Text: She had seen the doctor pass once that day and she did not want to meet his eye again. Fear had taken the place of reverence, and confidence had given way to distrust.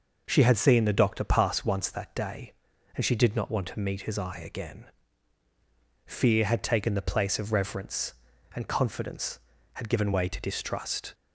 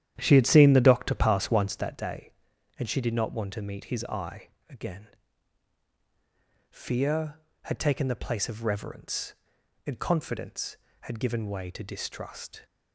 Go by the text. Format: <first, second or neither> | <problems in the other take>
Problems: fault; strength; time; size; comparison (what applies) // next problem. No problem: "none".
first | starts louder than the rest; strong; until 2.0 s; 10.5 dB // pauses between "eye" and "again"; slight; at 4.4 s; 0.20 s long